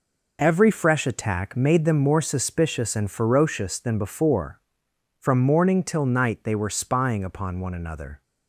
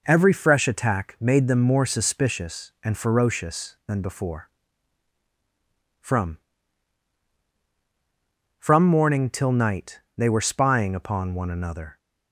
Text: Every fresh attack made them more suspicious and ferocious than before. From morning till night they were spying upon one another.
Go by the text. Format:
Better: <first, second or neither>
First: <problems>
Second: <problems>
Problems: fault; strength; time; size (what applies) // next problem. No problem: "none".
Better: first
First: none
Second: says "From" twice; at 8.5 s // pauses between "night" and "they"; slight; at 10.0 s; 0.16 s long